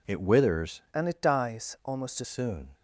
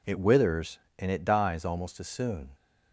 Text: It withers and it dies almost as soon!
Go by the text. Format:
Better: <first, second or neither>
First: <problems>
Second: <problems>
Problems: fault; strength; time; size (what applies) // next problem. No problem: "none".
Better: second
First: changes voice from "and" to "as"; from 0.9 to 2.2 s; 1.3 s long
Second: none